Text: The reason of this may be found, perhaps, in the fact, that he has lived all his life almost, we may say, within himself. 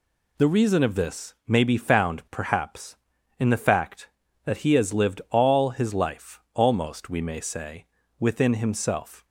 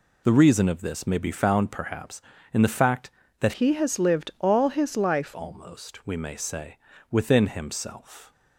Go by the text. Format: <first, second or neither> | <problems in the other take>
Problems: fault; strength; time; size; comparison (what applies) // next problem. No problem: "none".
first | changes voice from "he" to "life"; from 3.5 to 5.3 s; 1.8 s long